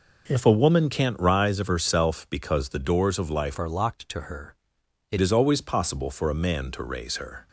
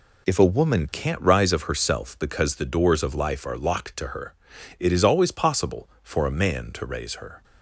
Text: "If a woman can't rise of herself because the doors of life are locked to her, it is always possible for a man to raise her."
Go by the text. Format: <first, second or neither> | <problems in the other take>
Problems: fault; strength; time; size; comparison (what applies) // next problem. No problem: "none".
second | changes voice from "are" to "it"; from 3.5 to 5.1 s; 1.6 s long